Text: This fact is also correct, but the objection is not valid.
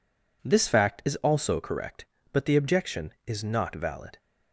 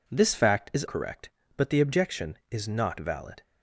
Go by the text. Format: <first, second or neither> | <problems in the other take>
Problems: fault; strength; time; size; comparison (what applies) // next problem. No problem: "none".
first | skips "also"; at 0.8 s